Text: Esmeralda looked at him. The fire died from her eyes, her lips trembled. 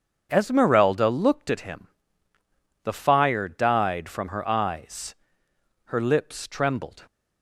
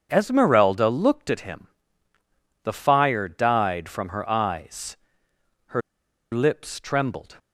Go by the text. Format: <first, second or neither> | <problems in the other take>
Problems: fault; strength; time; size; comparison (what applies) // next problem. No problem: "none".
first | starts louder than the rest; strong; until 1.1 s; 7.5 dB; strong in the first // pauses between "her" and "lips"; noticeable; at 5.8 s; 0.52 s long